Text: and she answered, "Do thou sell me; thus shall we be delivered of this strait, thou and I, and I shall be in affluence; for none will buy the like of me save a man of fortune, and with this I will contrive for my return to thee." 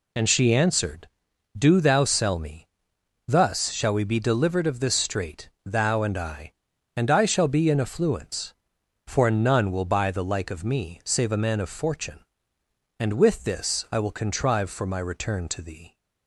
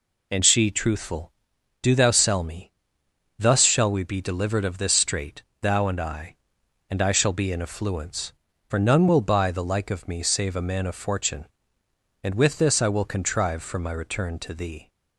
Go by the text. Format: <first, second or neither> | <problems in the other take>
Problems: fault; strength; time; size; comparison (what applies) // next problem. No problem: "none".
first | says "truthful" for "answered"; at 0.7 s